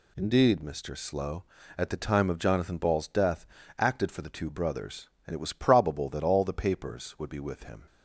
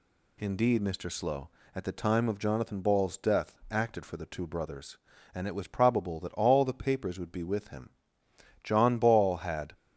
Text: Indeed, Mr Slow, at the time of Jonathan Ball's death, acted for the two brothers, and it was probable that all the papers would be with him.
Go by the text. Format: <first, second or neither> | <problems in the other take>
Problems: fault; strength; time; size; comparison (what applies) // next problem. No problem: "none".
first | goes on to say "John Ball had"; noticeable; from 8.6 s on; 1.1 s long